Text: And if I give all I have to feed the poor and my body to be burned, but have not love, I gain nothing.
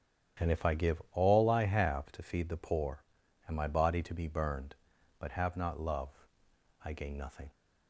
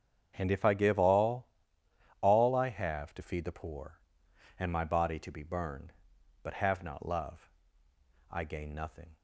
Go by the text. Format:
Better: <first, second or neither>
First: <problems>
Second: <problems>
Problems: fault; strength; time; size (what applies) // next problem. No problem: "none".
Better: first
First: starts louder than the rest; strong; until 1.5 s; 9.5 dB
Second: starts louder than the rest; strong; until 1.3 s; 8 dB // says "all" twice; at 2.2 s